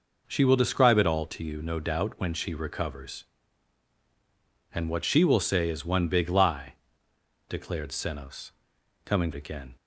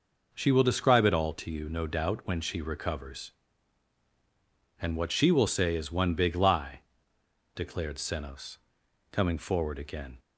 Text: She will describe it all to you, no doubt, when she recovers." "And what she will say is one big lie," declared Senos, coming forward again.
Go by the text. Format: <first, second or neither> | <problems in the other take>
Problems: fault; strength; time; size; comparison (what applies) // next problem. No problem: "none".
second | skips "forward"; at 9.3 s